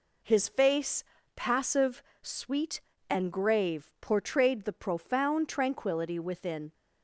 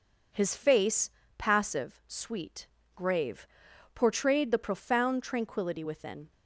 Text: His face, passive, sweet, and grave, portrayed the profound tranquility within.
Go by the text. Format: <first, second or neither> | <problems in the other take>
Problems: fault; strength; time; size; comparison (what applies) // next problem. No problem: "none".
first | skips "and"; at 2.8 s